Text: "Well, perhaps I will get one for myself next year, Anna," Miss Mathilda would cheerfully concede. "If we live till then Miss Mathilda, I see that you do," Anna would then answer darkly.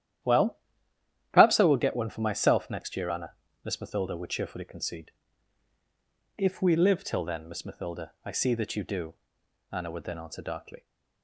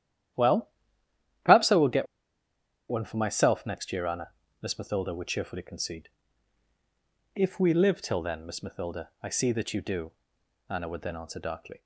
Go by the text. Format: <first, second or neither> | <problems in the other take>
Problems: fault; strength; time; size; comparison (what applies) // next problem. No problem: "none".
first | starts louder than the rest; strong; until 2.9 s; 11.5 dB; strong in the first // pauses between "get" and "one"; noticeable; at 2.0 s; 0.84 s long